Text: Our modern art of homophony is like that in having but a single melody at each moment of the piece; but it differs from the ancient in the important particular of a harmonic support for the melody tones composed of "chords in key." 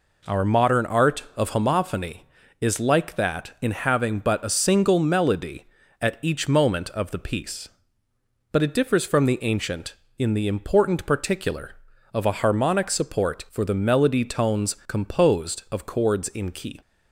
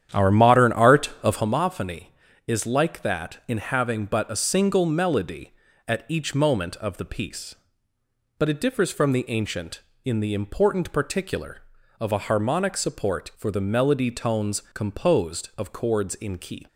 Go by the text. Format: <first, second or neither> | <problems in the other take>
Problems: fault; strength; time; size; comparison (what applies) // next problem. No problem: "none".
first | starts louder than the rest; strong; until 1.5 s; 9.5 dB